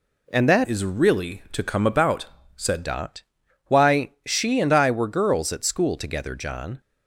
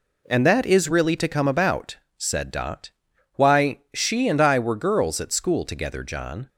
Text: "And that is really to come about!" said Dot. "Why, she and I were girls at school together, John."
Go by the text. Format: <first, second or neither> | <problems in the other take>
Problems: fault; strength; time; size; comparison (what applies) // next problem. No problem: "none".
second | changes voice from "is" to "said"; from 0.6 to 2.8 s; 2.2 s long